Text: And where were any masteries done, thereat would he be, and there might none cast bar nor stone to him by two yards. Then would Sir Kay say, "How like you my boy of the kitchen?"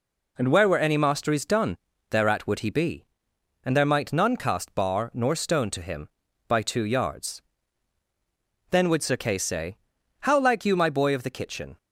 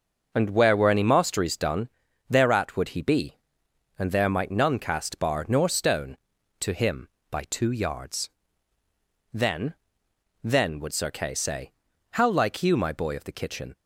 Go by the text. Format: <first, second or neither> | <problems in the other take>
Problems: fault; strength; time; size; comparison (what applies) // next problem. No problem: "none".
first | says "Then" twice; at 10.4 s